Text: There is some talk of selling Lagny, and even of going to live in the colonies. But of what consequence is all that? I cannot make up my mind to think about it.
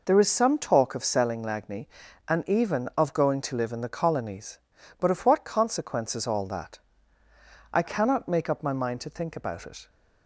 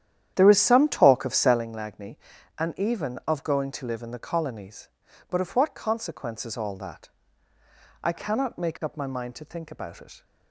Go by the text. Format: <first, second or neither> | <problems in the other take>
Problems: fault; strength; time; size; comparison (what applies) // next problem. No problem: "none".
first | starts louder than the rest; strong; until 1.7 s; 10.5 dB